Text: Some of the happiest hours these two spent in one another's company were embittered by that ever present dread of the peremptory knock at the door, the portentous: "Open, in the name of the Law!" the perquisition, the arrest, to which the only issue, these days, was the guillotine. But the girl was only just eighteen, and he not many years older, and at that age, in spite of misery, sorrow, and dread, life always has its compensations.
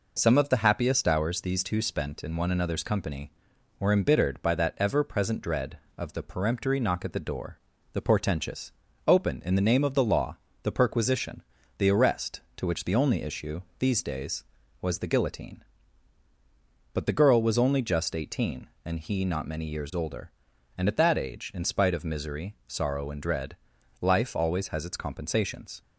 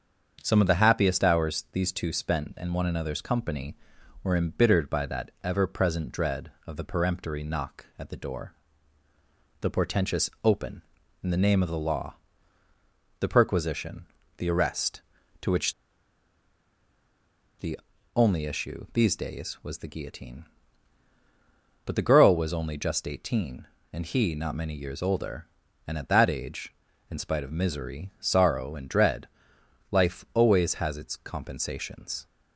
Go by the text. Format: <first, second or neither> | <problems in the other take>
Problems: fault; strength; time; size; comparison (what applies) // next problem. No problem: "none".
first | starts louder than the rest; until 1.4 s; 7 dB // pauses between "which" and "the"; strong; at 15.7 s; 1.8 s long // pauses between "the" and "only"; slight; at 17.7 s; 0.36 s long